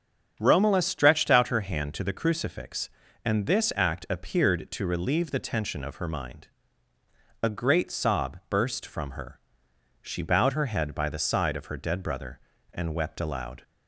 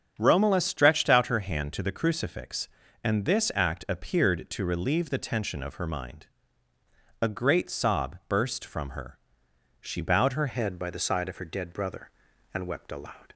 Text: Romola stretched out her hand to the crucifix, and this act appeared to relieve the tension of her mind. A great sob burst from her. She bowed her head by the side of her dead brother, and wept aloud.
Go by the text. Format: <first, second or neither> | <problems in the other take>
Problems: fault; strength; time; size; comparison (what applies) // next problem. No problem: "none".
first | starts louder than the rest; strong; until 1.2 s; 8 dB; strong in the first // changes voice at "head"; from 10.4 s on; 2.9 s long